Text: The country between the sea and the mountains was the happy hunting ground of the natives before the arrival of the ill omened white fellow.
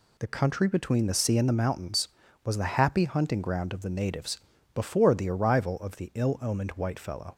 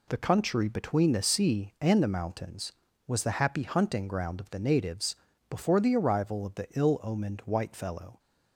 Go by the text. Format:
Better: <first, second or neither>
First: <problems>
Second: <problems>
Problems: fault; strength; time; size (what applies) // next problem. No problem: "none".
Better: neither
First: pauses between "natives" and "before"; slight; at 4.3 s; 0.34 s long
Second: pauses between "natives" and "before"; slight; at 5.1 s; 0.36 s long